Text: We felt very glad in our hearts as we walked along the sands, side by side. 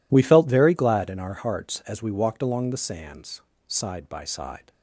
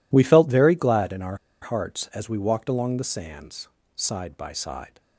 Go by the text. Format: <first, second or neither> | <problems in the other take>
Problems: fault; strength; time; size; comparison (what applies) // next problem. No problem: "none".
first | pauses between "our" and "hearts"; slight; at 1.3 s; 0.25 s long